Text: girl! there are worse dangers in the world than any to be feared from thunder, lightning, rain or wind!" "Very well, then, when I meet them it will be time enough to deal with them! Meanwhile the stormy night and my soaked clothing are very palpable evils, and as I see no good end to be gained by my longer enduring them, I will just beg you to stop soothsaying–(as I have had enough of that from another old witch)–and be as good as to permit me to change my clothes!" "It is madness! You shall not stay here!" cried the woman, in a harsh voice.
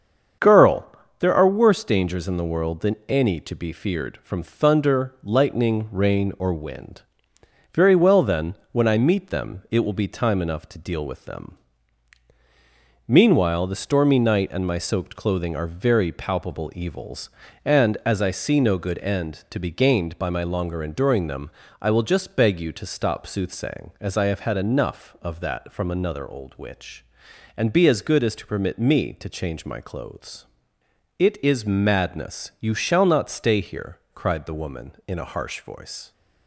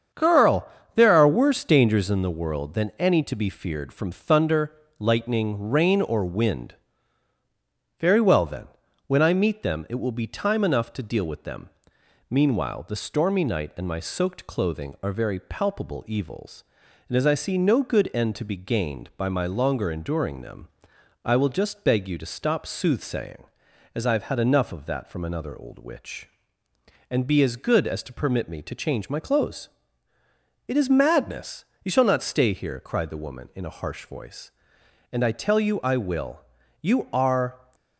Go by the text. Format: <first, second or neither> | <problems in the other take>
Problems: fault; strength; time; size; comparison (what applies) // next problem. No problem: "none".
first | starts louder than the rest; strong; until 1.4 s; 7.5 dB; strong in the first // goes on to say "And I tell you I will You are"; strong; from 35.1 s on; 2.5 s long